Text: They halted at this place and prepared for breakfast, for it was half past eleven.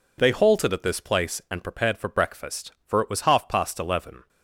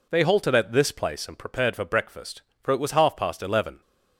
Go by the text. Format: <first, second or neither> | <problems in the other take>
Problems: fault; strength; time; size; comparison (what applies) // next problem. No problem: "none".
neither | none